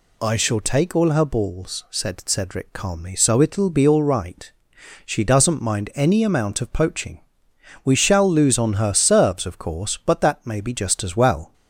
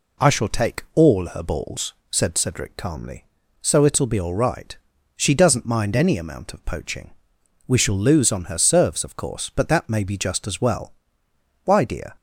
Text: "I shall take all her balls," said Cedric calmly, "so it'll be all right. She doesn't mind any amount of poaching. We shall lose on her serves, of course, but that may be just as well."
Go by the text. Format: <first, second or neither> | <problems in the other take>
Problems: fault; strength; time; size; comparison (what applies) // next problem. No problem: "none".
first | goes on to say "Why dear"; from 11.6 s on; 0.52 s long